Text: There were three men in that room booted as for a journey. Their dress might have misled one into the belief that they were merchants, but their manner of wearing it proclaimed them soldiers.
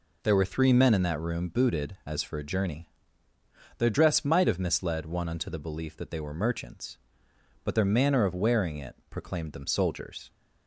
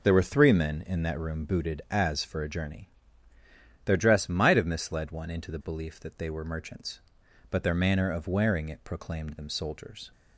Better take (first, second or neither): second